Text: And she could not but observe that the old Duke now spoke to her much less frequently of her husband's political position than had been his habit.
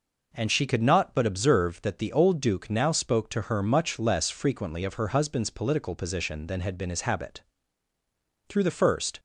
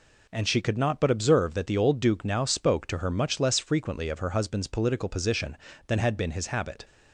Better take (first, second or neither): second